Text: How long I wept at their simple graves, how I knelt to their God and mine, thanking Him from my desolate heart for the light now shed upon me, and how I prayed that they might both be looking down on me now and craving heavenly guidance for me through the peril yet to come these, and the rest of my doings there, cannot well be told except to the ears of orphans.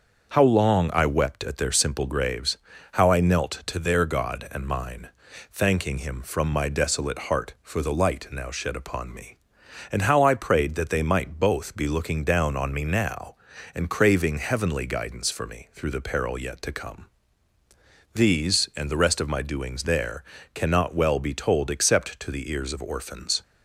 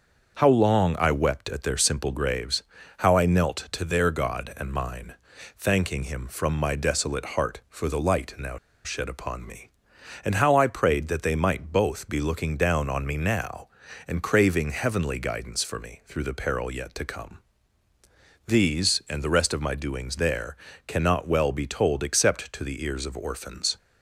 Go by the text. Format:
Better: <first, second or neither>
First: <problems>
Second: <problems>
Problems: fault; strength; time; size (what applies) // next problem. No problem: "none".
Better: first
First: starts louder than the rest; until 1.3 s; 6.5 dB // pauses between "come" and "these"; at 17.0 s; 1.0 s long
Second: starts louder than the rest; until 1.4 s; 6.5 dB // pauses between "now" and "shed"; slight; at 8.5 s; 0.28 s long // pauses between "come" and "these"; at 17.3 s; 1.0 s long